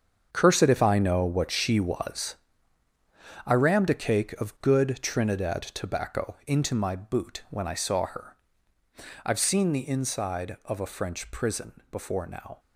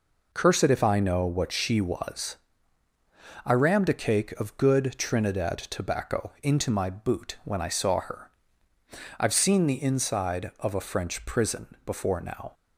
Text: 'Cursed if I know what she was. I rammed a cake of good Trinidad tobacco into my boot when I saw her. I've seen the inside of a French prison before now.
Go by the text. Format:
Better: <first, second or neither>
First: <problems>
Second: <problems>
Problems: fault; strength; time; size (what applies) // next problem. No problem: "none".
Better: second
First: gets quieter; strong; throughout; 12 dB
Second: none